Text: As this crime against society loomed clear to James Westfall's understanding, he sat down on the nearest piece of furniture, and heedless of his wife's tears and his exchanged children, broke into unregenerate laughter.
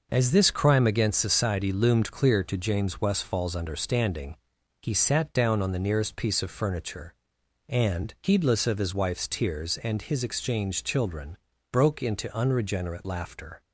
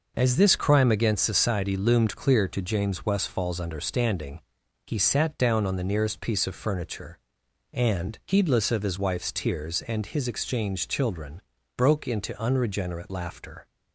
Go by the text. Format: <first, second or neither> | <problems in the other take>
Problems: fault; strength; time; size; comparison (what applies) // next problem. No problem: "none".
neither | none